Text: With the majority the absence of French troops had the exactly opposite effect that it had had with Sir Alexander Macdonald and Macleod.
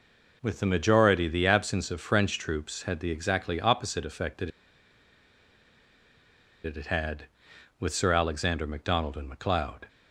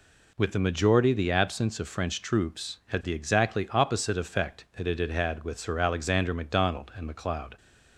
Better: second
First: pauses between "that" and "it"; strong; at 4.4 s; 2.1 s long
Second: none

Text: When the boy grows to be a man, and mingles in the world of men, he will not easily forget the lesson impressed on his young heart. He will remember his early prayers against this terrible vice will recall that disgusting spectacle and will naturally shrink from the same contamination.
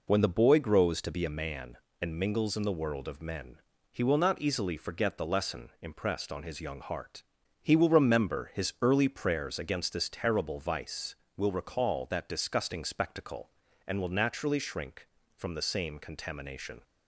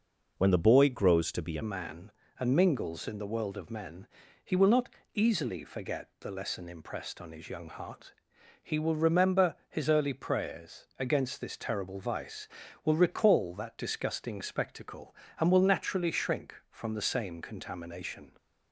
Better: first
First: none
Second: changes voice at "man"; from 1.6 s on; 16.7 s long // pauses between "not" and "easily"; slight; at 4.9 s; 0.24 s long // pauses between "remember" and "his"; slight; at 9.5 s; 0.16 s long

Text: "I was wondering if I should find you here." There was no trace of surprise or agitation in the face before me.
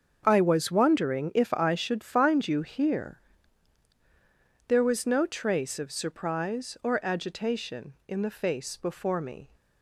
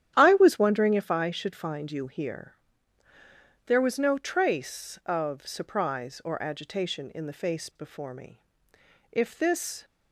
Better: first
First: starts louder than the rest; until 1.2 s; 7 dB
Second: starts louder than the rest; strong; until 1.1 s; 10.5 dB // goes on to say "If this"; noticeable; from 9.1 s on; 0.74 s long

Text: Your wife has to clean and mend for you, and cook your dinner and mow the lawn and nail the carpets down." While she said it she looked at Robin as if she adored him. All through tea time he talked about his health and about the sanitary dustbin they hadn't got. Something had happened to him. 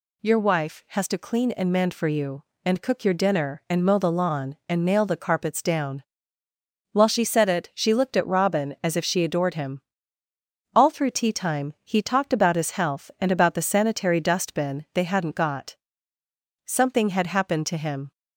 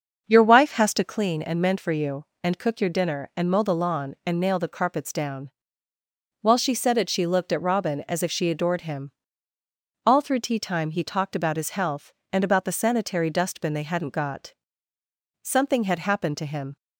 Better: first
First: none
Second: starts louder than the rest; until 1.2 s; 6.5 dB

